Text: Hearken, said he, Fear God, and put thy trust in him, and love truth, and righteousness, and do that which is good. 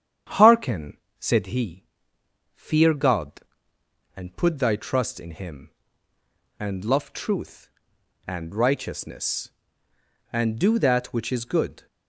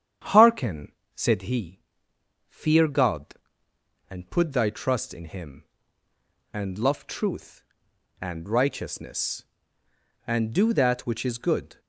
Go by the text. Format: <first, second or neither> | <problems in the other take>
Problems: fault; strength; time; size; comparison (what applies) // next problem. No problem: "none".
neither | starts louder than the rest; strong; the same in both